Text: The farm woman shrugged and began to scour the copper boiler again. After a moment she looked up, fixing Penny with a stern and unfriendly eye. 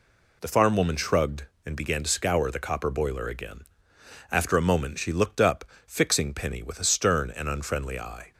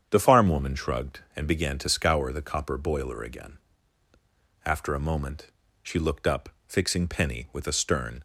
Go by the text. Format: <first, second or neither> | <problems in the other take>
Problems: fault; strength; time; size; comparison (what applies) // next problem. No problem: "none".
first | starts louder than the rest; strong; until 1.1 s; 8 dB // pauses between "moment" and "she"; slight; at 5.4 s; 0.34 s long // stops before "and unfriendly eye"; at 8.1 s